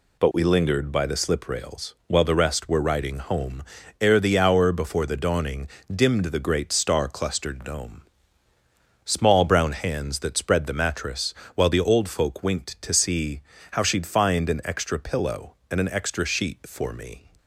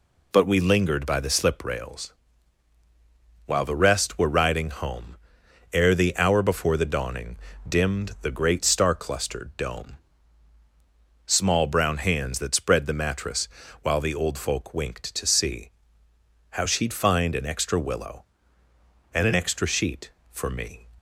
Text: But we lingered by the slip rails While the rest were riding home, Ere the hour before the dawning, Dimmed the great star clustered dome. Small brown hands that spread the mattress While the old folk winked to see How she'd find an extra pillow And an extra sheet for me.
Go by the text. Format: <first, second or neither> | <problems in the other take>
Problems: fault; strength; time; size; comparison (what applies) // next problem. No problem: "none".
first | pauses between "rails" and "While"; strong; at 2.1 s; 1.3 s long // pauses between "mattress" and "While"; slight; at 13.4 s; 0.34 s long; slight in the first // pauses between "see" and "How"; noticeable; at 15.6 s; 0.80 s long; slight in the first // says "willow" for "pillow"; at 17.7 s